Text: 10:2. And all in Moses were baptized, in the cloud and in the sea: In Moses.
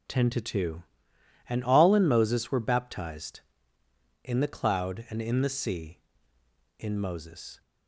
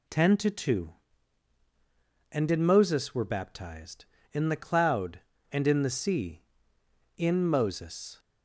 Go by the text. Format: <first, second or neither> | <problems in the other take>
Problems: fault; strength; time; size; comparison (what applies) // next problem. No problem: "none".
first | skips "all"; at 2.5 s